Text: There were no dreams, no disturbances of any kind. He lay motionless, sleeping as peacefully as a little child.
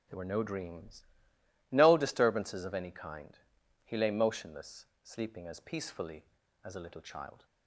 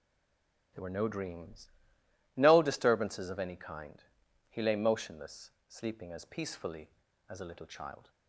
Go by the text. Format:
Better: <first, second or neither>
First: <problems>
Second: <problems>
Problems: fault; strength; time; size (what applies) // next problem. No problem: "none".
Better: first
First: none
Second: stays silent before the first word; slight; until 0.7 s; 0.7 s long